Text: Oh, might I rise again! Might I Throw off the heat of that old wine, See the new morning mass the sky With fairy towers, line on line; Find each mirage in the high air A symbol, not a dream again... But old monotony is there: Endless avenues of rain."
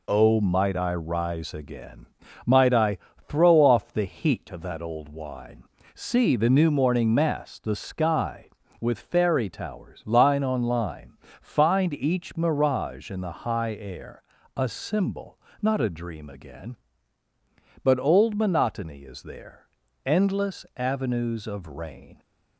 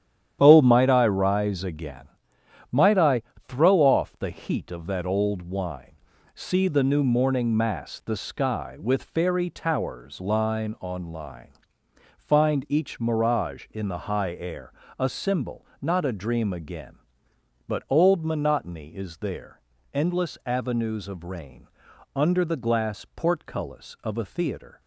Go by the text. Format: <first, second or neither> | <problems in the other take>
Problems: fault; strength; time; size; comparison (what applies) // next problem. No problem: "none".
first | starts louder than the rest; strong; until 1.4 s; 10 dB // pauses between "I" and "Throw"; slight; at 3.2 s; 0.24 s long; slight in the first // pauses between "air" and "A"; slight; at 14.7 s; 0.26 s long; slight in the first // goes on to say "Under the glass portcullis of a theatre"; strong; from 22.1 s on; 2.6 s long